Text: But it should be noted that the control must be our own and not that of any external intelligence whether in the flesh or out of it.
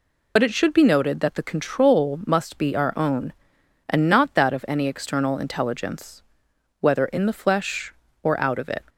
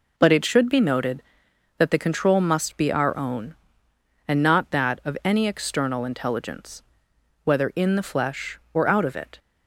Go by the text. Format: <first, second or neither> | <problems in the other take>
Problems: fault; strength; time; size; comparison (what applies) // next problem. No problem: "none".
second | loses the start of "But"; at 0.3 s; 45 ms // pauses between "intelligence" and "whether"; noticeable; at 6.2 s; 0.58 s long; noticeable in the second